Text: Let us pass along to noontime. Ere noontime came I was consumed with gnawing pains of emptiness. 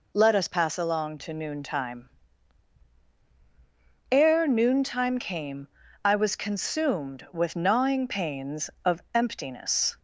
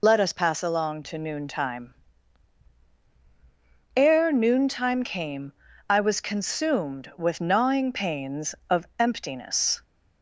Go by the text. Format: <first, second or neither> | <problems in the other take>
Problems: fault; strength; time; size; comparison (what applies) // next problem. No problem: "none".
first | loses the start of "Let"; at 0.0 s; 40 ms // pauses between "came" and "I"; slight; at 5.5 s; 0.34 s long; slight in the first